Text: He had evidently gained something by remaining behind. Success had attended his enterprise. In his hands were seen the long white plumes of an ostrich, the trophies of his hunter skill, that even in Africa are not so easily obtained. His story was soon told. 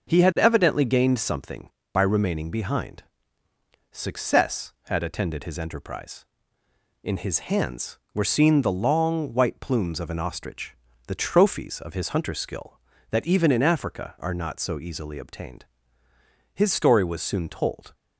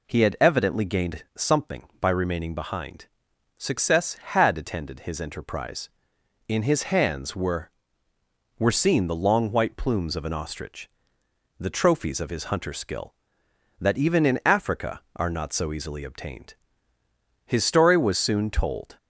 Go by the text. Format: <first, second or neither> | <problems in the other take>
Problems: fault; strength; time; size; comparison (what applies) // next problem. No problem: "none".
first | says "were" twice; at 8.5 s